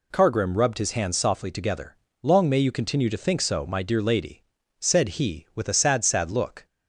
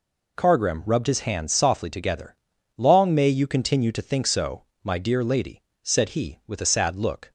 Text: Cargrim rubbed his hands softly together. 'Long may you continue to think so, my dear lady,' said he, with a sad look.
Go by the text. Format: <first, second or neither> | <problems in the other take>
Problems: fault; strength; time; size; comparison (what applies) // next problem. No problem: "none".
second | says "sad" twice; at 6.0 s